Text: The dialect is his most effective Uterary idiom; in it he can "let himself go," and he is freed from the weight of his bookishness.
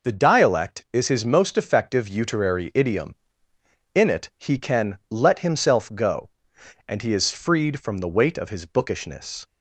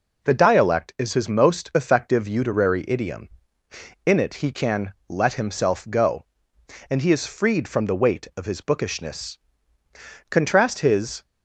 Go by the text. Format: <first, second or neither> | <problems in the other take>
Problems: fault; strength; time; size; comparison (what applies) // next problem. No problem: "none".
first | pauses between "can" and "let"; slight; at 4.9 s; 0.16 s long // goes on to say "Contrast his"; noticeable; from 10.2 s on; 0.94 s long